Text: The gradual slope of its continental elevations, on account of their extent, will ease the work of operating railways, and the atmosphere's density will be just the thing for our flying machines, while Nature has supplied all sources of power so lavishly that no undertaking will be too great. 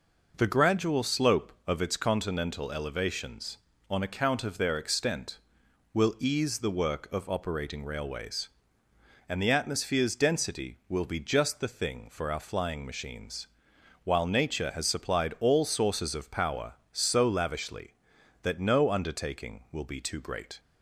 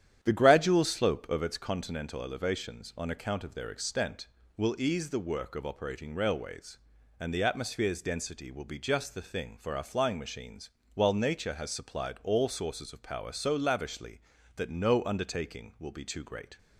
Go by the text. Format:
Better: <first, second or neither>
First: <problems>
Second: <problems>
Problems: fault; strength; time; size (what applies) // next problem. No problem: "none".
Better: first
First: none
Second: starts louder than the rest; strong; until 1.4 s; 10 dB